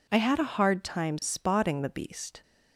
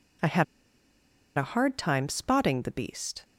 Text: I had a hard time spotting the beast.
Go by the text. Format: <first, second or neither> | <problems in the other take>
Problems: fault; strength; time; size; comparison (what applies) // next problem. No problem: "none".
first | pauses between "had" and "a"; noticeable; at 0.4 s; 0.93 s long